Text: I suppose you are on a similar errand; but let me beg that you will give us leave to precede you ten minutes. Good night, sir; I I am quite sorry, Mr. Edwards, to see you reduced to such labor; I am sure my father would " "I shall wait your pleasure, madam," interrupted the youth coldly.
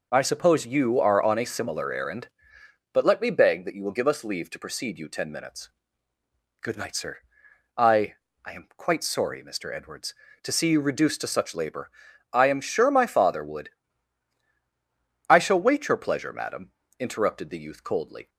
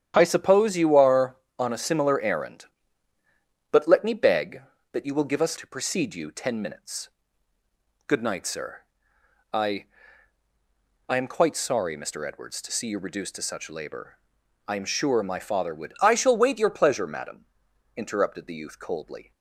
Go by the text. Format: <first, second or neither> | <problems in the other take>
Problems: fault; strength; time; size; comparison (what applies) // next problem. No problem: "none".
first | starts louder than the rest; strong; until 1.1 s; 9.5 dB // skips "leave"; at 5.5 s // pauses between "I" and "I"; at 9.8 s; 1.2 s long; slight in the first